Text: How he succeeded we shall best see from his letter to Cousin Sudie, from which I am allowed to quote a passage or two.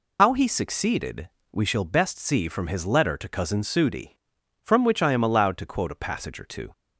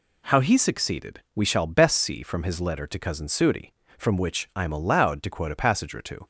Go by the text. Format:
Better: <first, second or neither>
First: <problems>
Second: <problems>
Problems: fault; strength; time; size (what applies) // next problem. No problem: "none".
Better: second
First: loses the start of "How"; at 0.1 s; 95 ms // pauses between "succeeded" and "we"; slight; at 1.2 s; 0.24 s long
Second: pauses between "succeeded" and "we"; slight; at 1.1 s; 0.16 s long